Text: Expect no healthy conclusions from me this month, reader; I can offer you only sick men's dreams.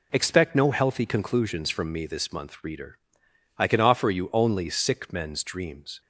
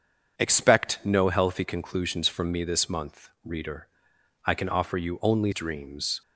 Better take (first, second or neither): first